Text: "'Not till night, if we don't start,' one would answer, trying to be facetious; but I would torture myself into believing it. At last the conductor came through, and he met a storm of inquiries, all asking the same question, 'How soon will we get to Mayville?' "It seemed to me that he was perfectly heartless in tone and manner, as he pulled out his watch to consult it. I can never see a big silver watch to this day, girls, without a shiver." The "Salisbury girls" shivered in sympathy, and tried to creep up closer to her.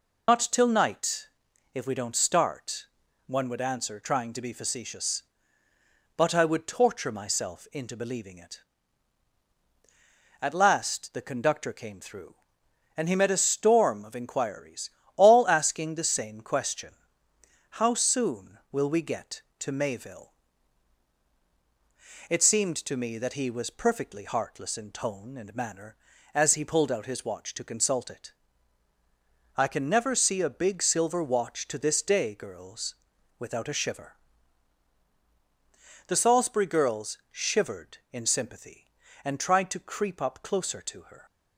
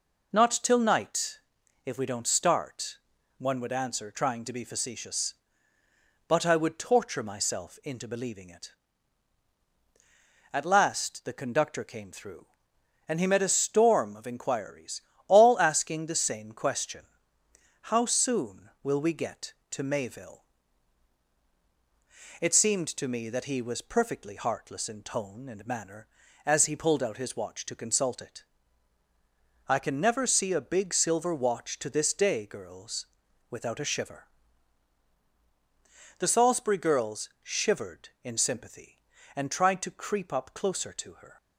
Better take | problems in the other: second | loses the start of "Not"; at 0.2 s; 70 ms

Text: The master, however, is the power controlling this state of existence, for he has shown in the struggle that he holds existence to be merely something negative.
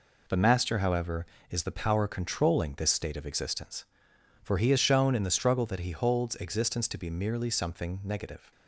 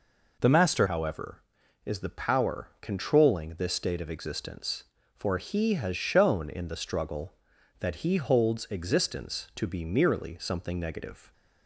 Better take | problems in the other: first | changes voice at "however"; from 0.8 s on; 10.5 s long

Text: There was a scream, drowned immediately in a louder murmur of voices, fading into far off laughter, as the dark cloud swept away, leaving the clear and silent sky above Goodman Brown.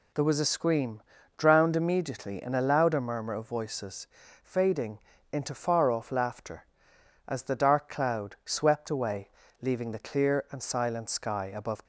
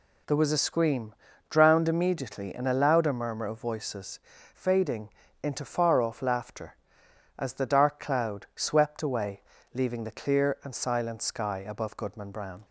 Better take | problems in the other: second | pauses between "fading" and "into"; slight; at 4.9 s; 0.32 s long; slight in the second // stops before "Goodman Brown"; at 11.8 s

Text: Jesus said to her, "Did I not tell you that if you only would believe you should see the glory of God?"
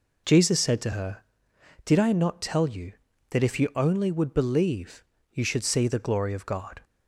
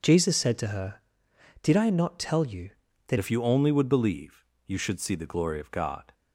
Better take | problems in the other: first | changes voice at "if"; from 3.1 s on; 3.0 s long // pauses between "believe" and "you"; slight; at 4.4 s; 0.22 s long; slight in the first

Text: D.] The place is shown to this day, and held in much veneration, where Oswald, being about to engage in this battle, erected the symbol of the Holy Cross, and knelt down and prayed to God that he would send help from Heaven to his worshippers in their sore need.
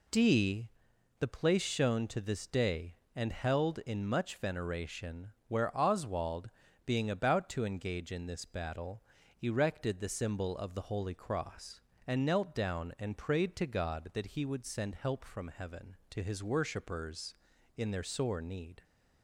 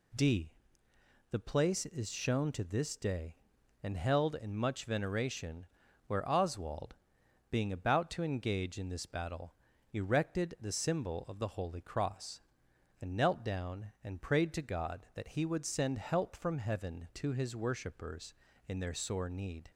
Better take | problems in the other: second | skips "is"; at 1.6 s

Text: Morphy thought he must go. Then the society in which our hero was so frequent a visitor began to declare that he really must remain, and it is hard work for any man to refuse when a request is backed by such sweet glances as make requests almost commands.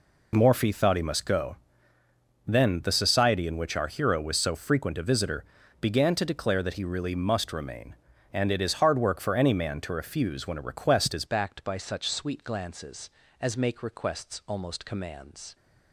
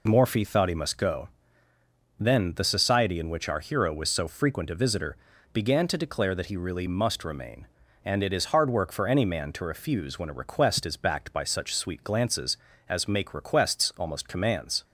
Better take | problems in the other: second | pauses between "visitor" and "began"; slight; at 5.4 s; 0.36 s long; slight in the second // changes voice at "backed"; from 11.2 s on; 4.3 s long

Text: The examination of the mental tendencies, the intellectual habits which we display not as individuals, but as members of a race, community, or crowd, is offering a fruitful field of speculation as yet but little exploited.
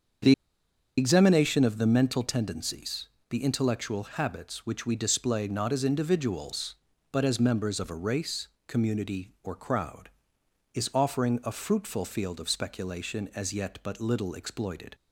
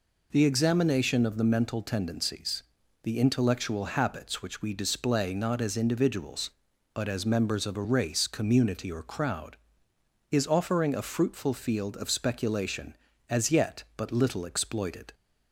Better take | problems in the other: second | starts louder than the rest; until 1.9 s; 7 dB // pauses between "The" and "examination"; noticeable; at 0.3 s; 0.66 s long

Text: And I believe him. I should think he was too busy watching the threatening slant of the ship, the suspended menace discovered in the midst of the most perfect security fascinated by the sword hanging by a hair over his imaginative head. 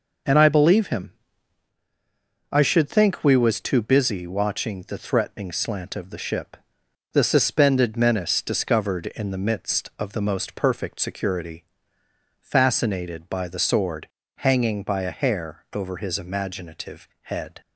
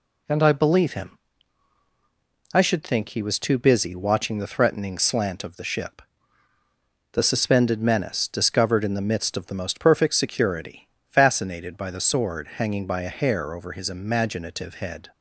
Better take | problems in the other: second | says "we" for "he"; at 3.2 s // pauses between "security" and "fascinated"; noticeable; at 11.6 s; 0.76 s long; slight in the second // pauses between "sword" and "hanging"; slight; at 14.0 s; 0.30 s long // pauses between "imaginative" and "head"; slight; at 17.0 s; 0.16 s long

